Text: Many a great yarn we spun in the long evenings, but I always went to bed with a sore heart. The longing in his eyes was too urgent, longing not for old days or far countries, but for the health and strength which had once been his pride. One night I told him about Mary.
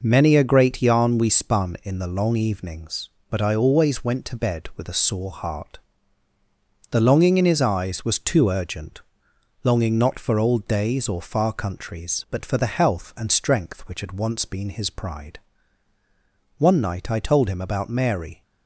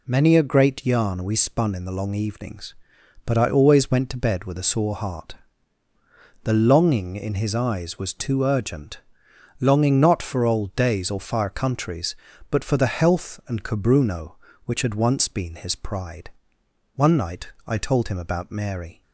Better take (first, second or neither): first